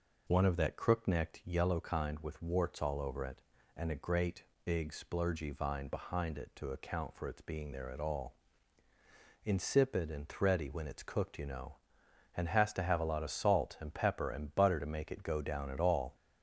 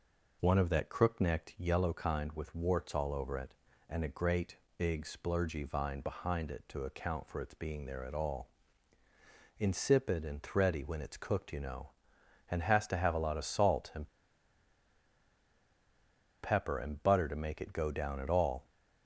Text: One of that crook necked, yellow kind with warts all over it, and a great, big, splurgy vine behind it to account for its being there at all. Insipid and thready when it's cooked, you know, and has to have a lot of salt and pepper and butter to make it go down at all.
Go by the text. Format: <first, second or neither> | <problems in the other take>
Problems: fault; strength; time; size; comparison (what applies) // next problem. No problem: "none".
first | pauses between "and" and "pepper"; strong; at 14.0 s; 2.3 s long